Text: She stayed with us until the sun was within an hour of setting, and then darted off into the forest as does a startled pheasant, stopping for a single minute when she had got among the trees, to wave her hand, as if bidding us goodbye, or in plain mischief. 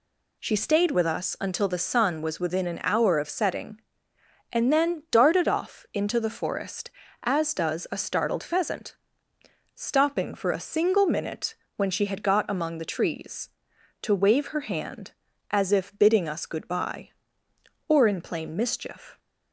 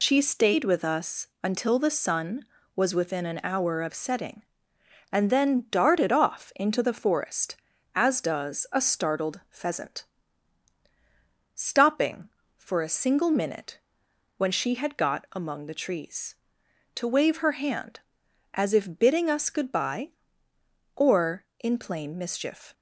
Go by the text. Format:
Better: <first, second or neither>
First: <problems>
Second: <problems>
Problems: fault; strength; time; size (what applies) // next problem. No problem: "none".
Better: first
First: pauses between "minute" and "when"; slight; at 11.5 s; 0.22 s long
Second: loses the start of "She"; at 0.0 s; 80 ms // pauses between "us" and "until"; slight; at 1.2 s; 0.16 s long // pauses between "minute" and "when"; noticeable; at 13.7 s; 0.62 s long